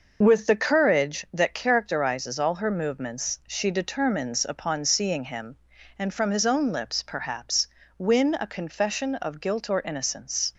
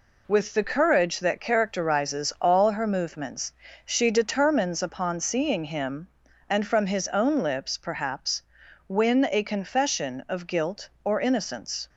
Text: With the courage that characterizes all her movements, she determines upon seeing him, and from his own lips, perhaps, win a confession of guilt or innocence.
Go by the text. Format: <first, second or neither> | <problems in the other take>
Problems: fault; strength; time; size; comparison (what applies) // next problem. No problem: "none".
neither | none